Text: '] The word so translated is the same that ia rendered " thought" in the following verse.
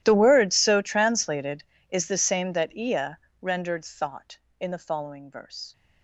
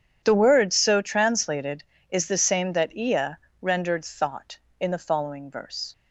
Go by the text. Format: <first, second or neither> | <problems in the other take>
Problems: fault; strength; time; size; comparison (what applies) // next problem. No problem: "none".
second | gets quieter; strong; throughout; 23 dB // starts louder than the rest; strong; until 1.0 s; 12.5 dB; strong in the second // pauses between "ia" and "rendered"; slight; at 3.1 s; 0.20 s long; slight in the second